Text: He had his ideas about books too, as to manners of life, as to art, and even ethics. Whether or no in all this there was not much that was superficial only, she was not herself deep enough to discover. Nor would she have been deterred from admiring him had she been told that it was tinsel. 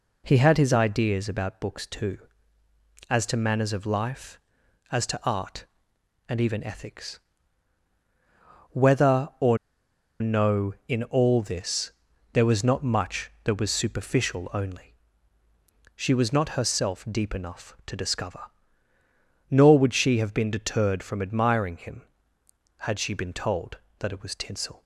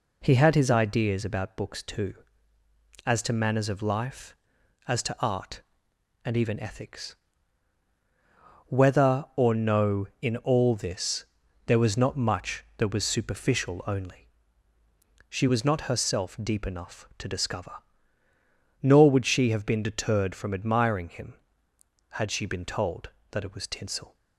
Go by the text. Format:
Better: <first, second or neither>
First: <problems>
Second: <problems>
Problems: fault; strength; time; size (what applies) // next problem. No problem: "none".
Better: second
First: pauses between "or" and "no"; noticeable; at 9.5 s; 0.64 s long // pauses between "this" and "there"; at 11.9 s; 0.40 s long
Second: pauses between "this" and "there"; at 11.2 s; 0.40 s long